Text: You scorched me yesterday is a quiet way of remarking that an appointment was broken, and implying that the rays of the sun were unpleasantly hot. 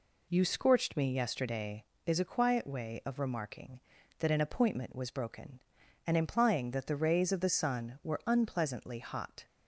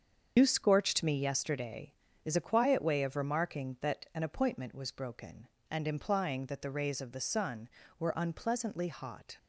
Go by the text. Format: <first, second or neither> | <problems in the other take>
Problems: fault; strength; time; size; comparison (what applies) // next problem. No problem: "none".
first | loses the start of "You"; at 0.3 s; 95 ms // starts louder than the rest; strong; until 1.3 s; 7 dB